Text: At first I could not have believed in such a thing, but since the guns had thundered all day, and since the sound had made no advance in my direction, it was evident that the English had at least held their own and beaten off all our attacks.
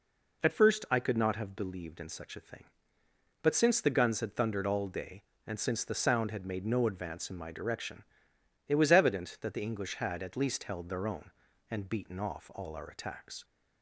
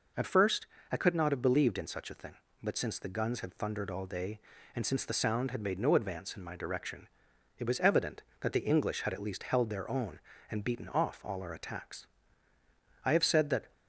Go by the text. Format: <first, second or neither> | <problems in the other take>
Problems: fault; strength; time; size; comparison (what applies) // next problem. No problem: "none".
first | pauses between "first" and "I"; slight; at 0.6 s; 0.24 s long // goes on to say "I have said that"; noticeable; from 13.0 s on; 0.68 s long